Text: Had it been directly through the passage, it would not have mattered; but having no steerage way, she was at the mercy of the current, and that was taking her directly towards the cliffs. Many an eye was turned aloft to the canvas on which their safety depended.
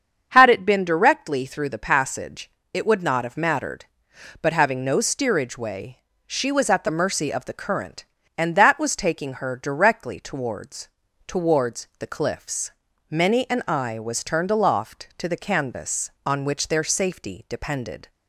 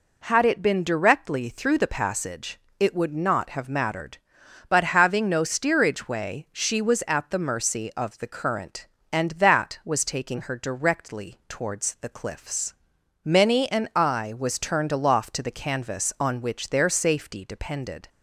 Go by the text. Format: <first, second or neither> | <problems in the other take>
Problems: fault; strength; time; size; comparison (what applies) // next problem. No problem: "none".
second | starts louder than the rest; strong; until 1.3 s; 7.5 dB // says "towards" twice; at 11.2 s